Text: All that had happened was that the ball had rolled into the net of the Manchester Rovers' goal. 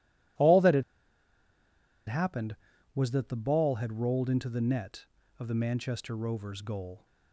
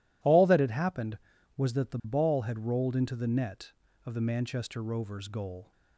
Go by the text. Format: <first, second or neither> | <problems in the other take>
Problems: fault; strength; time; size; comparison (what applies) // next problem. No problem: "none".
second | pauses between "had" and "happened"; at 0.8 s; 1.2 s long